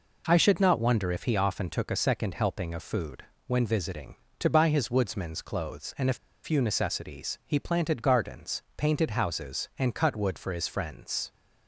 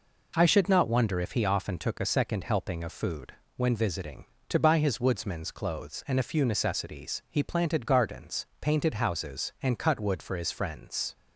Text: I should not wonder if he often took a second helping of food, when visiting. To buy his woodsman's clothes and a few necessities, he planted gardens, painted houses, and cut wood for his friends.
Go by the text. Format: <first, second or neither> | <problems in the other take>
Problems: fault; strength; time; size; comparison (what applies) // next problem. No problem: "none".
second | pauses between "a" and "few"; slight; at 6.1 s; 0.27 s long